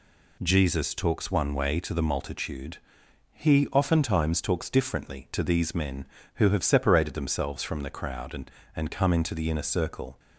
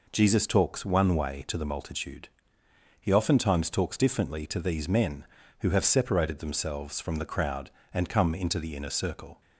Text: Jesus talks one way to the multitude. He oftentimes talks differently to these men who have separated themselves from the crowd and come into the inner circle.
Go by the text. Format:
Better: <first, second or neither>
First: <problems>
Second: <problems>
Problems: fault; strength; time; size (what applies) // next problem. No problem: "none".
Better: second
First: says "and" twice; at 8.7 s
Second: none